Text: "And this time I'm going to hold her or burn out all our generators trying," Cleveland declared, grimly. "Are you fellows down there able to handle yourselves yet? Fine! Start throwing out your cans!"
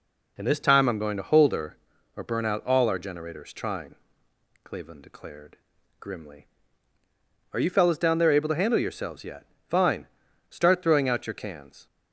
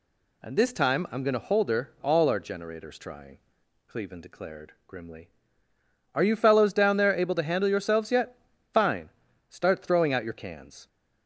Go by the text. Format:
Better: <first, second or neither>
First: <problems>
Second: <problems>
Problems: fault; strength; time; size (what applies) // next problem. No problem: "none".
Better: first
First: none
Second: skips "or burn out"; at 1.9 s